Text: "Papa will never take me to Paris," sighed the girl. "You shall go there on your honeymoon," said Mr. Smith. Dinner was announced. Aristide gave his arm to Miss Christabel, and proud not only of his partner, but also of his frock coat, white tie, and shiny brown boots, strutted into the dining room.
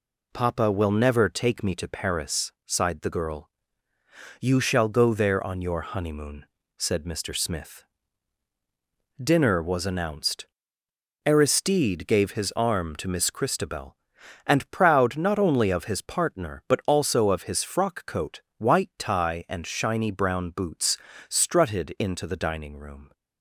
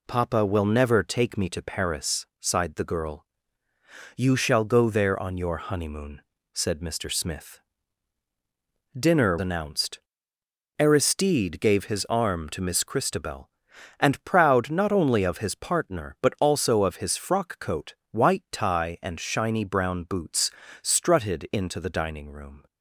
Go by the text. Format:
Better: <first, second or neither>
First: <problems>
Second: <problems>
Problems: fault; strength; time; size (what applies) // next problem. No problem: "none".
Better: first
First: none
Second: skips "was"; at 9.3 s